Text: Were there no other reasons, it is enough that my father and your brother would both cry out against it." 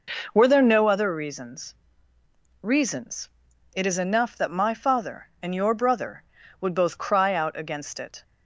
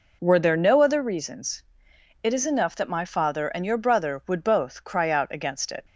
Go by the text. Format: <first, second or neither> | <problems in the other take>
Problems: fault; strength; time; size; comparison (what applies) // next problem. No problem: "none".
second | says "reasons" twice; at 2.6 s